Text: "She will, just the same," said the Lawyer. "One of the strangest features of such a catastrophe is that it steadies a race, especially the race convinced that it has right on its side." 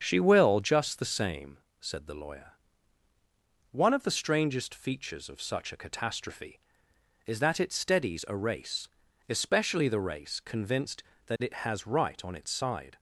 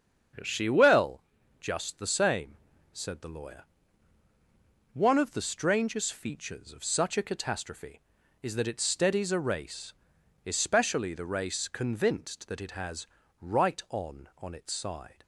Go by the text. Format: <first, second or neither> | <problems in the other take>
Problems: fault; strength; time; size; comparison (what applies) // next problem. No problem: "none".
first | starts louder than the rest; strong; until 1.8 s; 7 dB; strong in the first // pauses between "has" and "right"; slight; at 13.0 s; 0.34 s long // says "on" twice; at 14.3 s